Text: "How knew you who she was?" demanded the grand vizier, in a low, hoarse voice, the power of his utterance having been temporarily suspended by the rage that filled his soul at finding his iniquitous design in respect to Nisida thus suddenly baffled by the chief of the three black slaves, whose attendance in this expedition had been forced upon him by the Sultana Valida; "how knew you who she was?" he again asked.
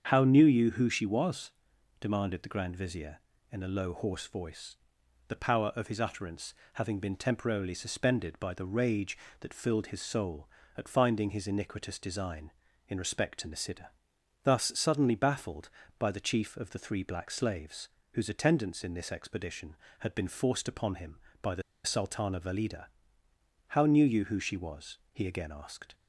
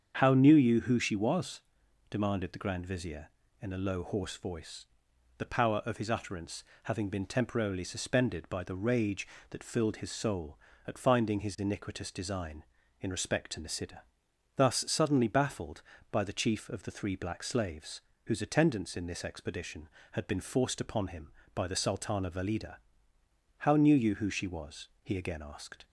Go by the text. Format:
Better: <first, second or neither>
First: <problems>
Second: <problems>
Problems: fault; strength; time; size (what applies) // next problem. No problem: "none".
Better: second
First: starts louder than the rest; strong; until 1.1 s; 7.5 dB // pauses between "utterance" and "having"; slight; at 6.5 s; 0.20 s long // pauses between "Nisida" and "thus"; noticeable; at 13.8 s; 0.54 s long // pauses between "the" and "Sultana"; slight; at 21.6 s; 0.24 s long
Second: starts louder than the rest; strong; until 1.2 s; 7.5 dB // pauses between "utterance" and "having"; slight; at 6.6 s; 0.20 s long // pauses between "Nisida" and "thus"; noticeable; at 14.0 s; 0.54 s long